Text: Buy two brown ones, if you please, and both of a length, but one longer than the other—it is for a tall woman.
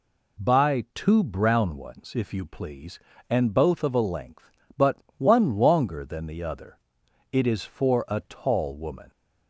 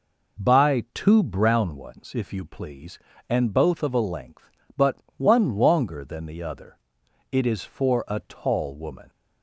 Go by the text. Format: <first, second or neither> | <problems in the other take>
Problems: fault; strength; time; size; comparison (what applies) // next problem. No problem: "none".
first | starts louder than the rest; noticeable; until 1.6 s; 5 dB // pauses between "but" and "one"; slight; at 4.9 s; 0.20 s long; slight in the first